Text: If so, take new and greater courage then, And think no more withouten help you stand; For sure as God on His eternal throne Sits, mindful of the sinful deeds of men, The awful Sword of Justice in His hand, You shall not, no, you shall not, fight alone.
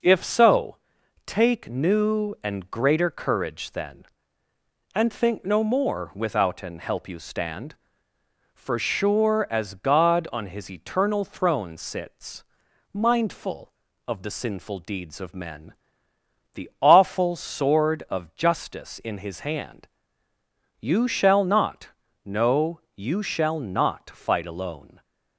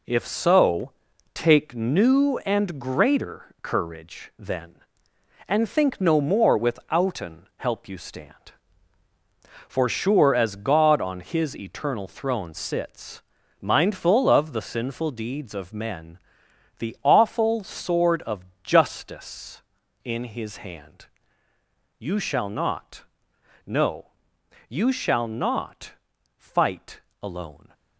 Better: first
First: none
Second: gets quieter; throughout; 7 dB // pauses between "of" and "Justice"; slight; at 18.4 s; 0.18 s long // pauses between "fight" and "alone"; slight; at 27.0 s; 0.22 s long

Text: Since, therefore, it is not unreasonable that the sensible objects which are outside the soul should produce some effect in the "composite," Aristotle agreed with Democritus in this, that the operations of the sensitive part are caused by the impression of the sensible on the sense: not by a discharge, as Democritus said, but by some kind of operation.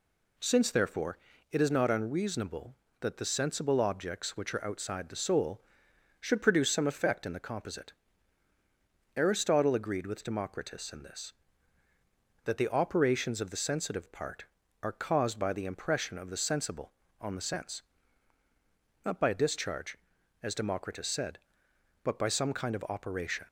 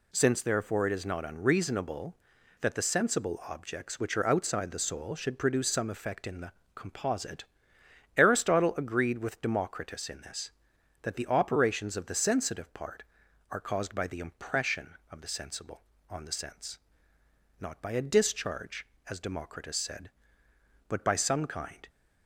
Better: first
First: none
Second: pauses between "the" and "composite"; slight; at 6.5 s; 0.22 s long // stops before "of operation"; at 21.8 s

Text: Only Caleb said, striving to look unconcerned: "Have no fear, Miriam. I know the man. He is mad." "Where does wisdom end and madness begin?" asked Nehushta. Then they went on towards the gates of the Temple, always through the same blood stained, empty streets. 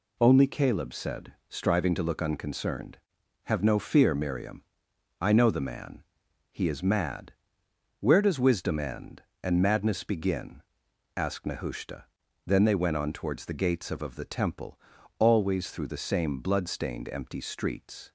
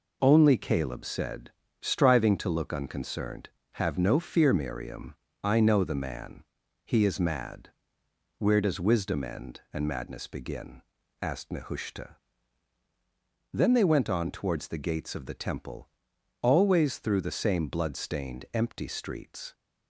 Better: second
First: says "of" twice; at 14.0 s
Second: none

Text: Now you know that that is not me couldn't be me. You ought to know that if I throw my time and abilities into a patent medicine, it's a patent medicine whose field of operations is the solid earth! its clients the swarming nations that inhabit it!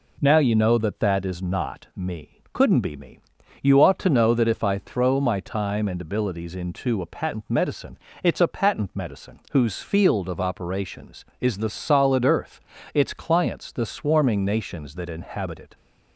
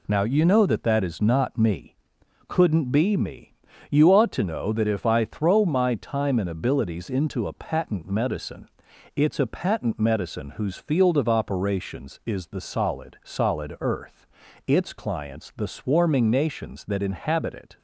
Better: first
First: pauses between "me" and "couldn't"; slight; at 2.3 s; 0.16 s long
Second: pauses between "me" and "couldn't"; noticeable; at 1.9 s; 0.54 s long // says "solid" twice; at 13.2 s

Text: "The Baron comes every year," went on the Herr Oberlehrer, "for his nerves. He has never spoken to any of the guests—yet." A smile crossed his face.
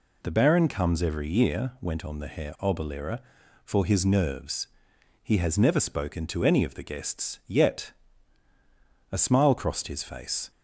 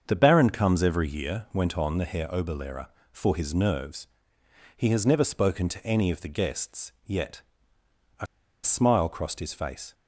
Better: first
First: none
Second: starts louder than the rest; until 1.0 s; 7 dB // pauses between "A" and "smile"; at 8.2 s; 0.37 s long

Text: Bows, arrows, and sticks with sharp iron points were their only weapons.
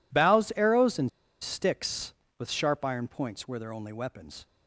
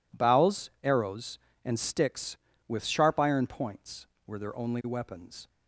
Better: second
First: pauses between "and" and "sticks"; slight; at 1.0 s; 0.31 s long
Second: none

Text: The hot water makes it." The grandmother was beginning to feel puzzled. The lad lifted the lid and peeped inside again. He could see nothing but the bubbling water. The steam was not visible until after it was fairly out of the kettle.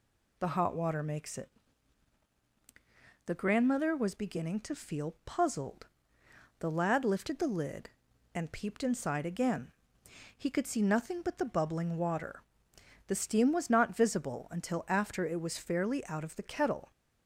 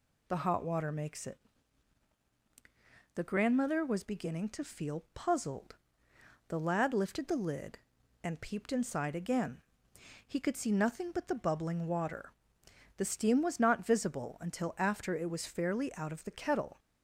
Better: neither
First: none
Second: none

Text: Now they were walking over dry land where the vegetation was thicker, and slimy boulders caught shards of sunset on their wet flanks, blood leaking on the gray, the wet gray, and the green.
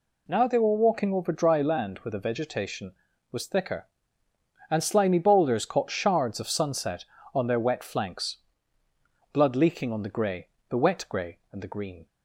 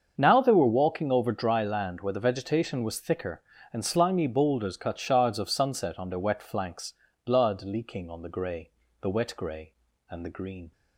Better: first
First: none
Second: starts louder than the rest; until 1.1 s; 7 dB // says "cut" for "caught"; at 4.7 s

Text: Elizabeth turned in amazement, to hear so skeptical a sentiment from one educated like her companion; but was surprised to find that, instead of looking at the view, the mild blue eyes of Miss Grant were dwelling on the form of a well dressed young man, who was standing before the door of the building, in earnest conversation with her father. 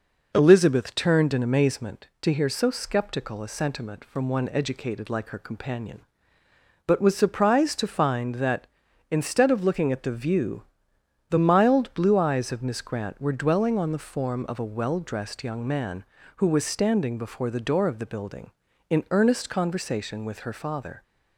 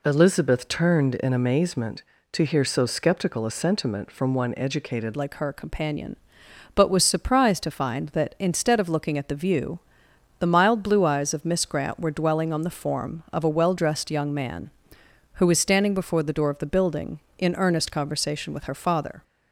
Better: first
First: none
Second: changes voice at "like"; from 5.1 s on; 14.1 s long

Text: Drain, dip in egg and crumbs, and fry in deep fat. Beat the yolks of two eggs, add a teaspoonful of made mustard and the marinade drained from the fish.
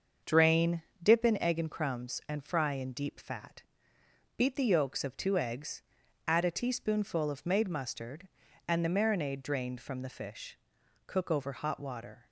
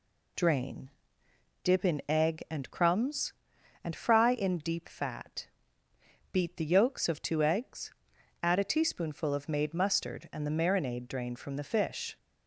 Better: second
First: starts louder than the rest; until 1.4 s; 6.5 dB // goes on to say "Cook over hot water"; noticeable; from 11.0 s on; 1.2 s long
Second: none

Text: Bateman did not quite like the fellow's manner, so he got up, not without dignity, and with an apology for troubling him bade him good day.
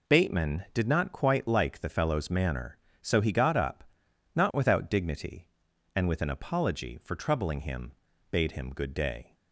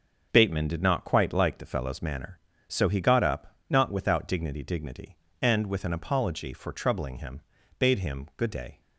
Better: first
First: pauses between "him" and "bade"; at 7.9 s; 0.40 s long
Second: says "dignity" twice; at 4.6 s // pauses between "him" and "bade"; at 7.3 s; 0.40 s long

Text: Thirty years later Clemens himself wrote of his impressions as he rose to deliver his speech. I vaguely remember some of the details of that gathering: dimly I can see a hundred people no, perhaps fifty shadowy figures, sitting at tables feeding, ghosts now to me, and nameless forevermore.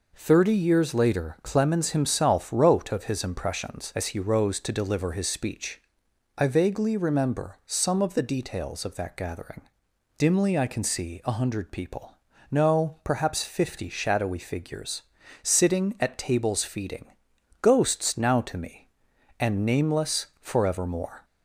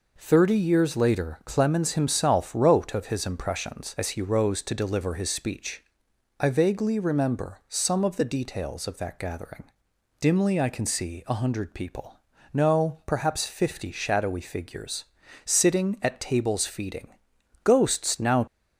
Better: first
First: pauses between "people" and "no"; at 12.1 s; 0.38 s long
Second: pauses between "people" and "no"; at 12.1 s; 0.38 s long // stops before "to me and nameless forevermore"; at 18.4 s

